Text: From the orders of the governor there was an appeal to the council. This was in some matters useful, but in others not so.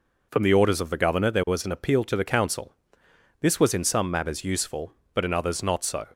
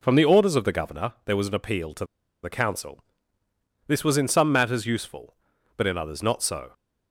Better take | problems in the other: first | pauses between "to" and "the"; at 2.0 s; 0.39 s long

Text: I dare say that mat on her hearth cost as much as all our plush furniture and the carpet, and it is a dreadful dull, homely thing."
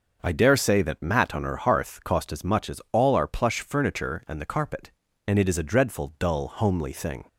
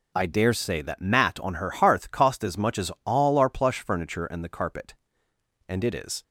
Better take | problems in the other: first | stops before "a dreadful dull homely thing"; at 6.2 s

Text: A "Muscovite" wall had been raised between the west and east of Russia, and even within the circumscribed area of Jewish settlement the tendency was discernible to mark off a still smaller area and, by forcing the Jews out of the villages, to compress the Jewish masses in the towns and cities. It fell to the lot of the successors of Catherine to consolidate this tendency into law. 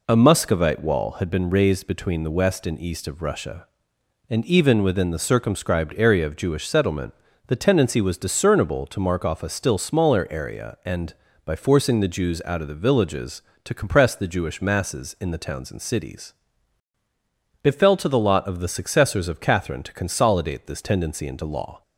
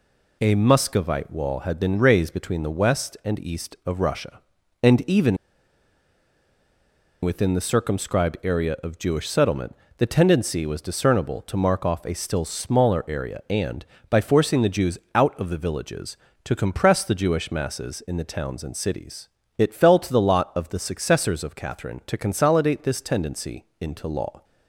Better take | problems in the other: first | pauses between "even" and "within"; strong; at 5.3 s; 1.8 s long // pauses between "settlement" and "the"; slight; at 9.7 s; 0.24 s long; slight in the first // pauses between "Jews" and "out"; slight; at 14.9 s; 0.16 s long // pauses between "tendency" and "into"; slight; at 23.6 s; 0.16 s long

